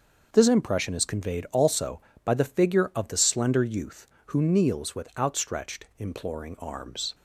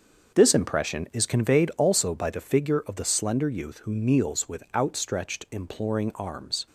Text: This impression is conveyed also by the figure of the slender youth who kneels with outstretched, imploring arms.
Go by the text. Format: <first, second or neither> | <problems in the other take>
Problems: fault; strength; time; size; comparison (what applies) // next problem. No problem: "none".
neither | starts louder than the rest; the same in both